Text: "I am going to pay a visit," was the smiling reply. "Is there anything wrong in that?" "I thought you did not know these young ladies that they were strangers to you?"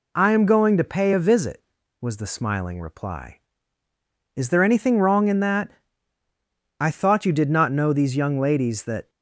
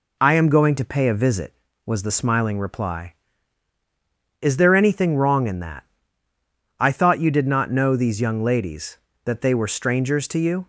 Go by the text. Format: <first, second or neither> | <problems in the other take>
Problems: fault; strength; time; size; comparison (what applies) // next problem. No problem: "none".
second | stops before "they were strangers to you"; at 9.0 s